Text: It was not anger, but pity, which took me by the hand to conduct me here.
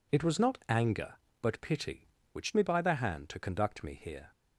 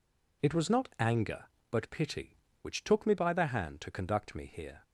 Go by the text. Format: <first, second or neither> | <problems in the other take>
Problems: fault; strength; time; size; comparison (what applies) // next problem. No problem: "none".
second | skips "took"; at 2.5 s